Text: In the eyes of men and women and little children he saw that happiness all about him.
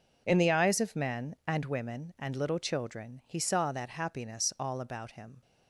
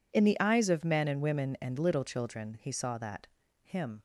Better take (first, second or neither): first